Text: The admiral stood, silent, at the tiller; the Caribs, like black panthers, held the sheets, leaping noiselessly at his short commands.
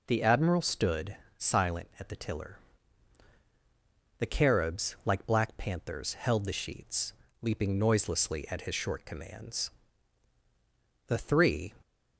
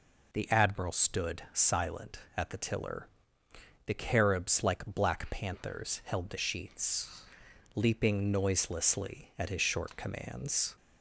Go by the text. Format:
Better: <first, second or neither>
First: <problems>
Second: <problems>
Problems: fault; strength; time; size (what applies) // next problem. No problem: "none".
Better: second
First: goes on to say "The three"; noticeable; from 11.0 s on; 0.68 s long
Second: none